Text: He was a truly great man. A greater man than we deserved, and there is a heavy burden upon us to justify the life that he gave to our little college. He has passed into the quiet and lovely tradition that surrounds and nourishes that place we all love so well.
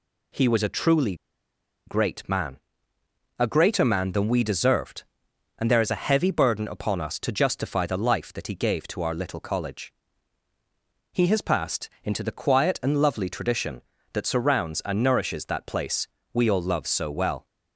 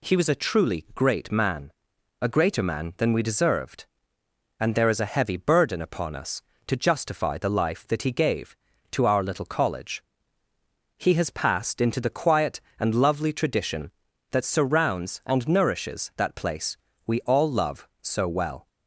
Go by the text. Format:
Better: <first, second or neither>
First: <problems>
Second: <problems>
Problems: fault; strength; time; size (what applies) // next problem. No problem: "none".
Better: second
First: pauses between "truly" and "great"; noticeable; at 1.1 s; 0.71 s long // pauses between "passed" and "into"; slight; at 11.8 s; 0.16 s long // pauses between "place" and "we"; slight; at 16.0 s; 0.26 s long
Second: pauses between "place" and "we"; slight; at 16.7 s; 0.28 s long